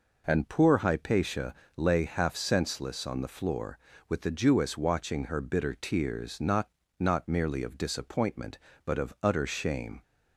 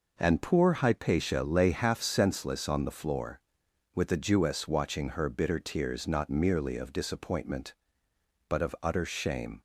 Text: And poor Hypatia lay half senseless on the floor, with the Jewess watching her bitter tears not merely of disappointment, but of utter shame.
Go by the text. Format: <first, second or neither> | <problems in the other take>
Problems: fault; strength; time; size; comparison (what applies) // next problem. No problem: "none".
second | pauses between "Hypatia" and "lay"; slight; at 1.5 s; 0.24 s long // says "not" twice; at 6.9 s